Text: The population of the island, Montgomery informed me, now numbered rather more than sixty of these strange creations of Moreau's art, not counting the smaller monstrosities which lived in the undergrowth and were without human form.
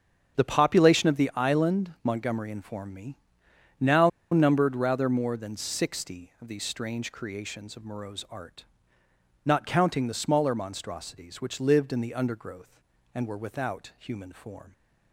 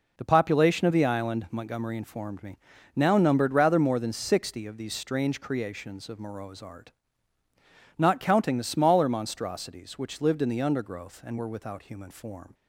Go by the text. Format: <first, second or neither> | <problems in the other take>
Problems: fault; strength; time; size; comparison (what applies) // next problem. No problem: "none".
second | starts louder than the rest; strong; until 1.4 s; 7.5 dB // pauses between "now" and "numbered"; slight; at 4.0 s; 0.24 s long